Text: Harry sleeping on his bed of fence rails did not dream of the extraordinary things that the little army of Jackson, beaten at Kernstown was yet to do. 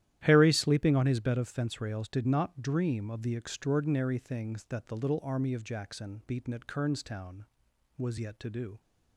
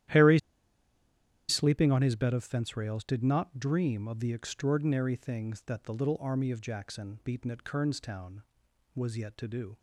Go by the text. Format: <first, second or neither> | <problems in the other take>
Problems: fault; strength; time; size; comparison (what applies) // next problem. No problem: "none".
first | starts louder than the rest; strong; until 2.2 s; 12 dB; strong in the first // pauses between "Harry" and "sleeping"; at 0.3 s; 1.0 s long